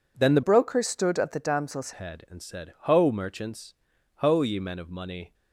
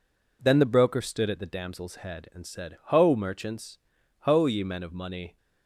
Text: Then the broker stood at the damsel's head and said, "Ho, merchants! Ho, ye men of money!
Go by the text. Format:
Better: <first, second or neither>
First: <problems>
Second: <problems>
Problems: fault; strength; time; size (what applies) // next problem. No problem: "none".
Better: second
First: changes voice from "broker" to "damsel's"; from 0.4 to 1.9 s; 1.5 s long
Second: none